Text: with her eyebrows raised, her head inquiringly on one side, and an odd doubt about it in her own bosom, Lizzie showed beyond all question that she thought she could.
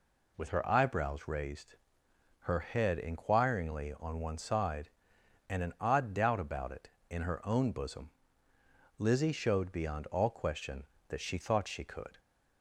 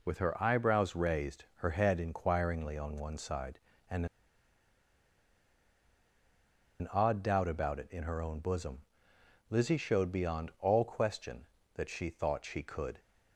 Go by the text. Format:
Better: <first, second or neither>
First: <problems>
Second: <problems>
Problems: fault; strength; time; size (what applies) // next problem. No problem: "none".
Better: first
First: none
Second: pauses between "and" and "an"; strong; at 4.0 s; 2.7 s long